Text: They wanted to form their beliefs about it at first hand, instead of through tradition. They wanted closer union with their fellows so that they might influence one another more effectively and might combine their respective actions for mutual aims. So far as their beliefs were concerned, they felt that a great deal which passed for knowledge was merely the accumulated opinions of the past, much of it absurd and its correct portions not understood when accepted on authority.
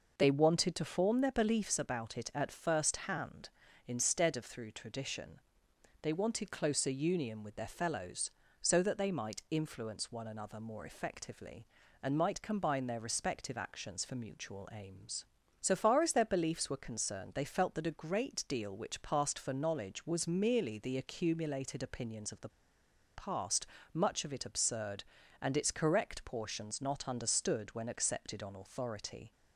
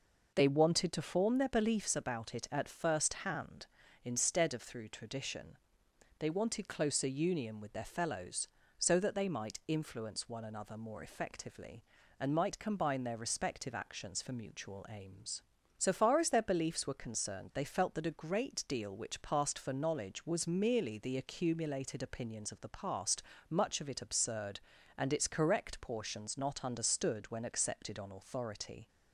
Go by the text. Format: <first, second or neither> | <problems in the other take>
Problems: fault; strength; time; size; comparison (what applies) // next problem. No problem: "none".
second | pauses between "the" and "past"; noticeable; at 22.4 s; 0.64 s long